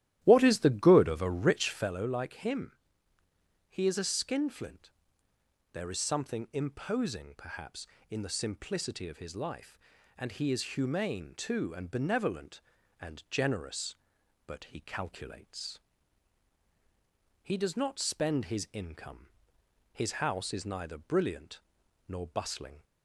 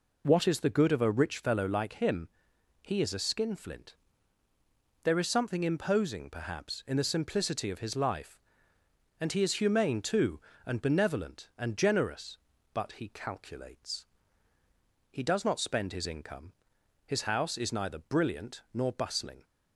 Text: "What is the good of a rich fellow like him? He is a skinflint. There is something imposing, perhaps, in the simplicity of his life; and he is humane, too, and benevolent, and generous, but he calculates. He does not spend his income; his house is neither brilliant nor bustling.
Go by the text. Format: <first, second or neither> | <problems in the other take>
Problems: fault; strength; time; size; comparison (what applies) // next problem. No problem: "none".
second | starts louder than the rest; strong; until 1.9 s; 13.5 dB // pauses between "brilliant" and "nor"; noticeable; at 21.6 s; 0.46 s long